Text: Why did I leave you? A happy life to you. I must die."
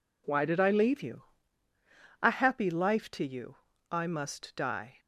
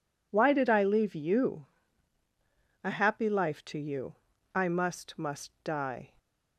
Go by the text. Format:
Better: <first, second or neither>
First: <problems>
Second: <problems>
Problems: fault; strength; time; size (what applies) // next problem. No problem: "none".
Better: first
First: none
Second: says "must" twice; at 5.1 s